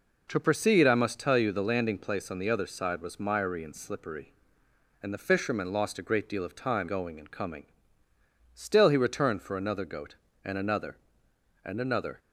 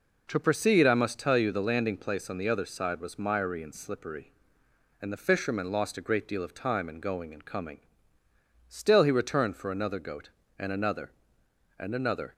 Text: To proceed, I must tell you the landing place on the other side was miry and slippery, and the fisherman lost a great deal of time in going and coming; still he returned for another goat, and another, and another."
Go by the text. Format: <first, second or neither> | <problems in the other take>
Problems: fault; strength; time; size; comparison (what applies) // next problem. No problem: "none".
second | skips "in"; at 6.8 s